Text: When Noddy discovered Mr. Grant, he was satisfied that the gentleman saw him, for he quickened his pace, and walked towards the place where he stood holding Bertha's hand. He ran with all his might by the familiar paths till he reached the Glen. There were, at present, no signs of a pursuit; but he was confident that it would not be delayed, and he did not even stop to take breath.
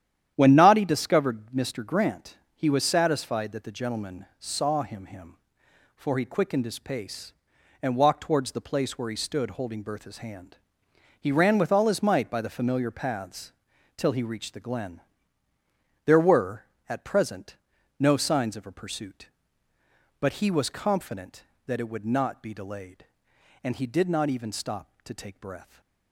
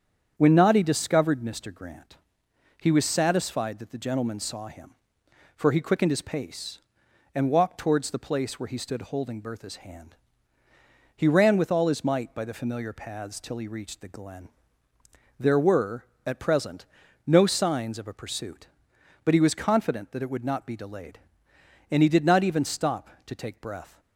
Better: second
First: starts louder than the rest; strong; until 1.3 s; 10.5 dB // says "him" twice; at 5.0 s // pauses between "paths" and "till"; at 13.5 s; 0.44 s long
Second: starts louder than the rest; strong; until 1.3 s; 8 dB

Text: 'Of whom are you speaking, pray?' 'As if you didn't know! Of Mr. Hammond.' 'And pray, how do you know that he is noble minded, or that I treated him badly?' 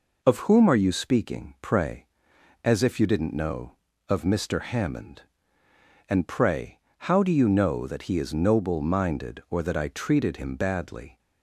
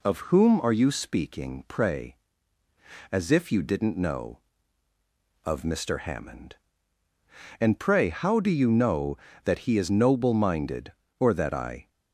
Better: first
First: none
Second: stops before "treated him badly"; at 11.8 s

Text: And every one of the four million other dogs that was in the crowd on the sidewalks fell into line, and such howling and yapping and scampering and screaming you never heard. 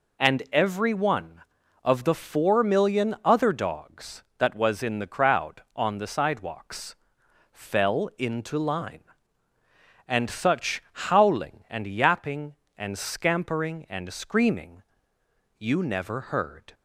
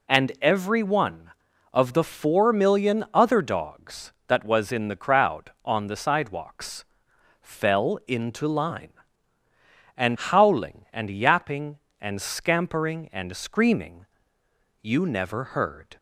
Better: first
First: pauses between "sidewalks" and "fell"; noticeable; at 6.9 s; 0.56 s long // pauses between "screaming" and "you"; noticeable; at 14.8 s; 0.76 s long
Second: pauses between "sidewalks" and "fell"; noticeable; at 6.8 s; 0.56 s long // skips "such"; at 10.1 s // pauses between "screaming" and "you"; noticeable; at 14.0 s; 0.76 s long

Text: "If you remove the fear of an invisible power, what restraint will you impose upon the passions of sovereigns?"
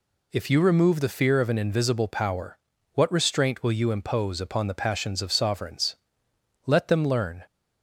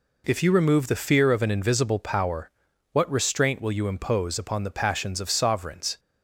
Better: second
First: goes on to say "Let them learn"; noticeable; from 6.6 s on; 0.80 s long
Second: none

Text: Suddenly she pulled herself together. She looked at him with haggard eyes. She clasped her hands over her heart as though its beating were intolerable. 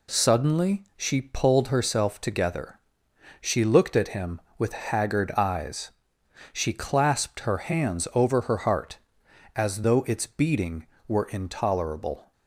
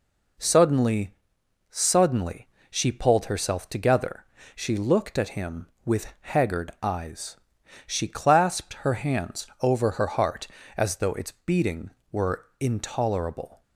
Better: first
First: none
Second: says "Suddenly" twice; at 1.6 s

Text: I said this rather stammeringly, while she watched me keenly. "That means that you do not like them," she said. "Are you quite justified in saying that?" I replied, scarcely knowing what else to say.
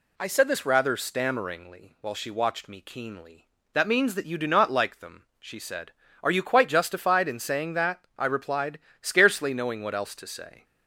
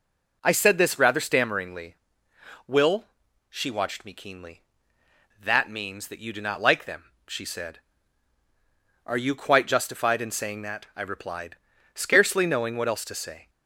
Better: first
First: none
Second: says "will" for "while"; at 2.6 s

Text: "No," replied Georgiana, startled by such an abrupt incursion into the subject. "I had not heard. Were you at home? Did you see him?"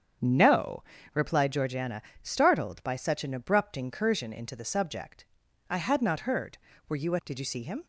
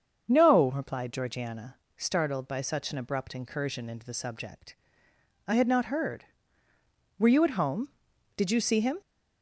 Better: second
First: starts louder than the rest; strong; until 1.5 s; 7.5 dB // skips "home"; at 7.2 s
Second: starts louder than the rest; until 1.2 s; 6.5 dB

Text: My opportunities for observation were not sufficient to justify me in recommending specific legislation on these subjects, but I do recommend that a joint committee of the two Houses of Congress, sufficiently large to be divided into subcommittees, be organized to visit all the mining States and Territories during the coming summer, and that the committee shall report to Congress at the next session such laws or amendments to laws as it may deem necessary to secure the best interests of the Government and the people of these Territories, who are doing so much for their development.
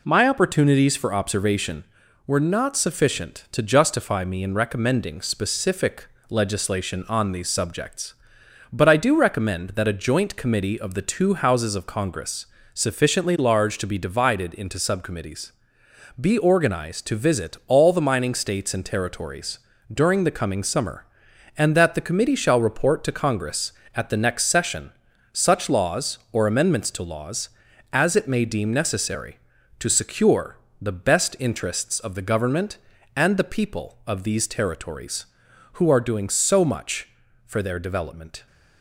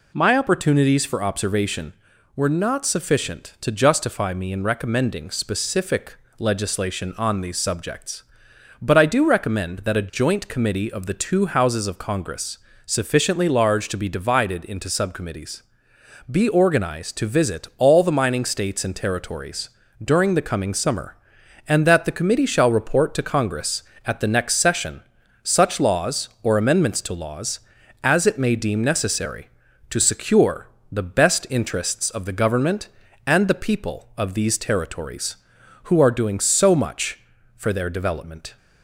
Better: second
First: gets quieter; throughout; 4 dB // pauses between "specific" and "legislation"; slight; at 6.0 s; 0.20 s long // pauses between "Territories" and "during"; slight; at 19.5 s; 0.34 s long // pauses between "session" and "such"; at 24.9 s; 0.40 s long // pauses between "secure" and "the"; slight; at 30.5 s; 0.24 s long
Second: pauses between "specific" and "legislation"; slight; at 6.1 s; 0.20 s long // pauses between "Territories" and "during"; slight; at 19.6 s; 0.34 s long // pauses between "session" and "such"; at 25.0 s; 0.40 s long // pauses between "secure" and "the"; slight; at 30.6 s; 0.24 s long

